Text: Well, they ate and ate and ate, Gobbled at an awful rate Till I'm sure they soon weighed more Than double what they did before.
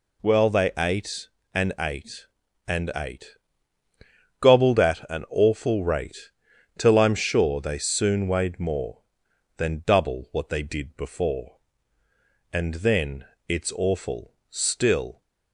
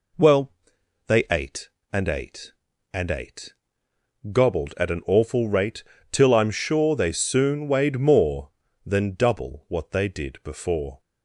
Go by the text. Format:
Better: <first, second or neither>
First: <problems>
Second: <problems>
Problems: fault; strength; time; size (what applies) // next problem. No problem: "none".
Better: second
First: pauses between "rate" and "Till"; noticeable; at 6.2 s; 0.48 s long // goes on to say "And then it's awful still"; strong; from 12.5 s on; 2.7 s long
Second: pauses between "rate" and "Till"; slight; at 5.8 s; 0.28 s long